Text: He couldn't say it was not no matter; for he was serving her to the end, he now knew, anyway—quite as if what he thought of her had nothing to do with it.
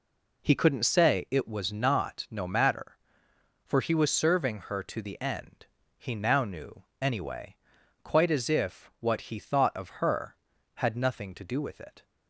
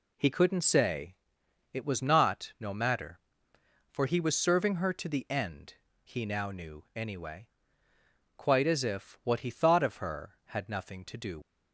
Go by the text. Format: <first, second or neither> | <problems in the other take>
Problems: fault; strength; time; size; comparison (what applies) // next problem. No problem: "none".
first | pauses between "say" and "it"; noticeable; at 1.1 s; 0.56 s long // stops before "with it"; at 11.4 s